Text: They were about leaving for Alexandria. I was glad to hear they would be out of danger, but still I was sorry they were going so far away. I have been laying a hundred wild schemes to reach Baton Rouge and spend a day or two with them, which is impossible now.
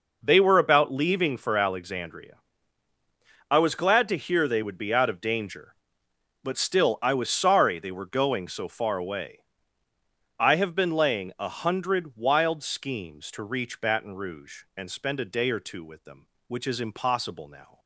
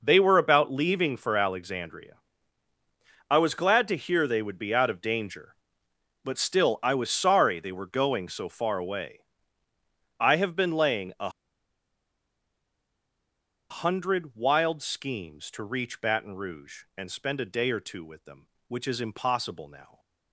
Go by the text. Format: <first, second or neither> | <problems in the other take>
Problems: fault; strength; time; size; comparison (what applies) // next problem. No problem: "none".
first | pauses between "a" and "hundred"; strong; at 11.2 s; 2.4 s long